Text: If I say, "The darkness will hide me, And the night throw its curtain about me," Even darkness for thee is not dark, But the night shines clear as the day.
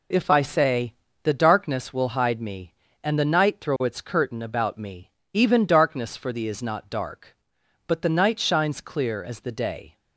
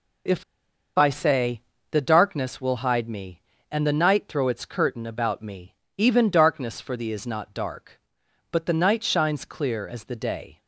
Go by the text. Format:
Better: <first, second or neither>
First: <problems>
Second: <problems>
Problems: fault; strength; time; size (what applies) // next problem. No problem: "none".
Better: first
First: none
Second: pauses between "If" and "I"; noticeable; at 0.4 s; 0.53 s long